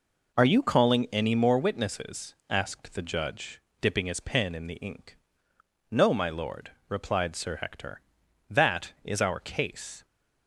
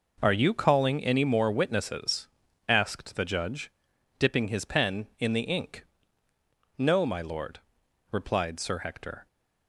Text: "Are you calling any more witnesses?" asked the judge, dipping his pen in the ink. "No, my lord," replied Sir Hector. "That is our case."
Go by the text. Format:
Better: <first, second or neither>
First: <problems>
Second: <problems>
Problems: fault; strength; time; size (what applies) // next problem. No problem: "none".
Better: first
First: none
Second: stops before "That is our case"; at 9.2 s